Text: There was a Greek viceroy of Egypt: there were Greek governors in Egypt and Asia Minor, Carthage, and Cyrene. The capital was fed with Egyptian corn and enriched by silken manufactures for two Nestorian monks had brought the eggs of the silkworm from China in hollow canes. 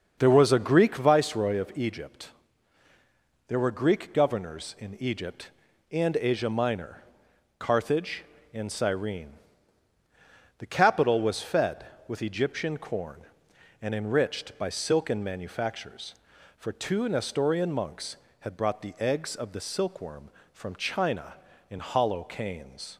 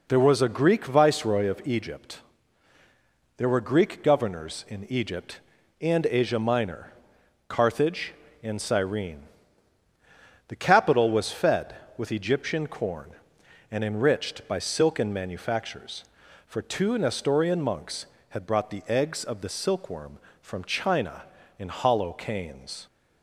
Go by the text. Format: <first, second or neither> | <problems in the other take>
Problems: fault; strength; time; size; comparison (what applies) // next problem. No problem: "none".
second | starts louder than the rest; until 1.1 s; 6.5 dB